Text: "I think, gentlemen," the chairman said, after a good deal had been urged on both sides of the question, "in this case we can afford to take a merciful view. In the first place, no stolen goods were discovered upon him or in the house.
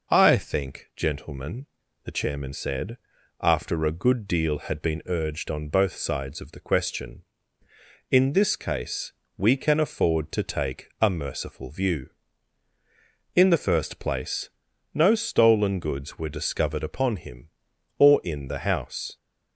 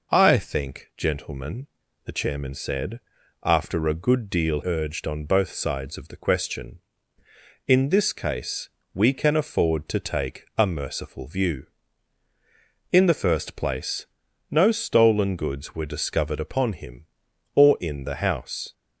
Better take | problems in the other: first | skips "had been"; at 4.6 s // pauses between "case" and "we"; slight; at 8.6 s; 0.24 s long; slight in the first

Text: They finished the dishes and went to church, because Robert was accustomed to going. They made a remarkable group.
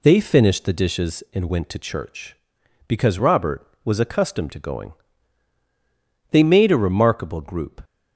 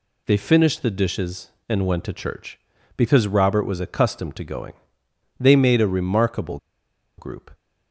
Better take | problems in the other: first | pauses between "remarkable" and "group"; noticeable; at 6.5 s; 0.60 s long

